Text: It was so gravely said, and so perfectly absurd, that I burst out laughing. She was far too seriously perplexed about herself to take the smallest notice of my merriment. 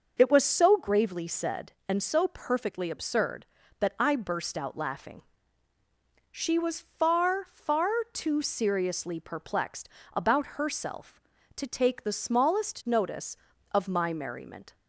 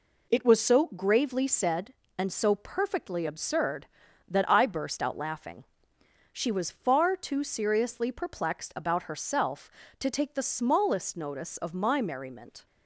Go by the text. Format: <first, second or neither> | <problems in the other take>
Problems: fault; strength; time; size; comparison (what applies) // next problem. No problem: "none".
second | says "far" twice; at 7.4 s // pauses between "perplexed" and "about"; slight; at 9.8 s; 0.26 s long